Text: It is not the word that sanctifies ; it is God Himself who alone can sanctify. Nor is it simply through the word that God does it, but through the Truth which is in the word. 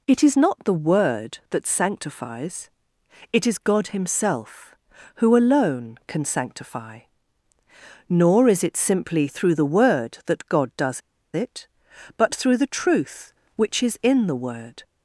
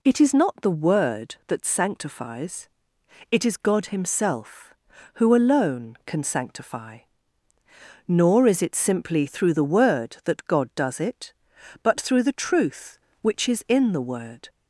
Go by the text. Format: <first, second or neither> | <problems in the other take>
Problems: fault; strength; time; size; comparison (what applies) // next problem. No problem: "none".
second | pauses between "does" and "it"; slight; at 11.0 s; 0.33 s long